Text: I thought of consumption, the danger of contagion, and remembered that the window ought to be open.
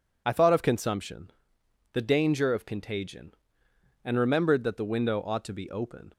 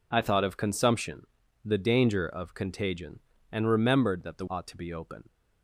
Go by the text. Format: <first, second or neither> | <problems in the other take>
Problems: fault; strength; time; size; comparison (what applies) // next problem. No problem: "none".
first | skips "window"; at 4.4 s